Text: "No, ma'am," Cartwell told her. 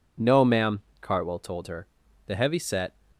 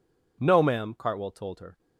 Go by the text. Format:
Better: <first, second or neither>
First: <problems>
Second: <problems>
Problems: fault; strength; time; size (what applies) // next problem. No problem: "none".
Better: second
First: goes on to say "The heavy set"; noticeable; from 2.2 s on; 0.66 s long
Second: none